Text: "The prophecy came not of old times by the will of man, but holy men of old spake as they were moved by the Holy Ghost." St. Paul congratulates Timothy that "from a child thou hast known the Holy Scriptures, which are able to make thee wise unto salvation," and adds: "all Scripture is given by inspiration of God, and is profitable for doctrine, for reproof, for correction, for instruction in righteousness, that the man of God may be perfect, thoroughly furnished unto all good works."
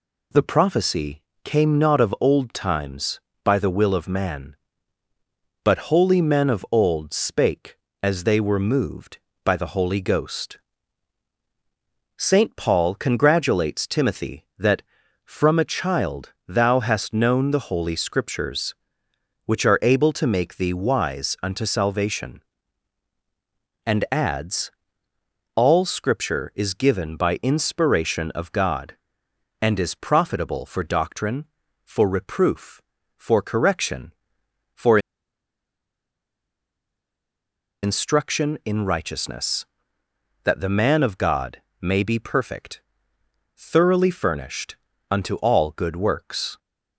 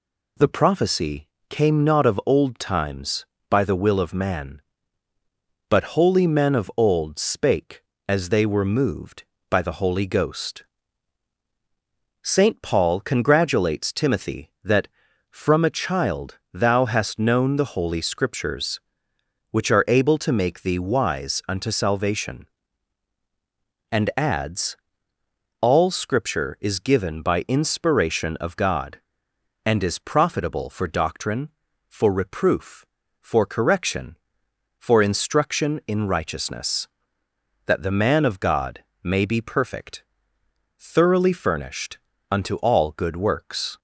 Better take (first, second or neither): second